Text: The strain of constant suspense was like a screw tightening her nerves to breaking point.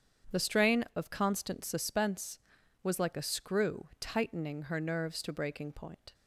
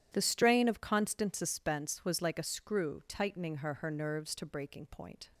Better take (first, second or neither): first